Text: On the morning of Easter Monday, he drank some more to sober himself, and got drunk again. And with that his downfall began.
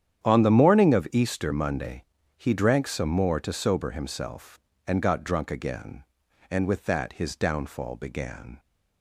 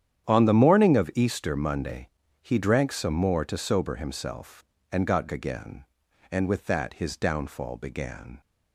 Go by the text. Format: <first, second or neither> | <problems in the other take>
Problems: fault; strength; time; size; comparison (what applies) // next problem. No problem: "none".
first | starts louder than the rest; strong; until 1.2 s; 9.5 dB; strong in the first // skips "drunk"; at 5.2 s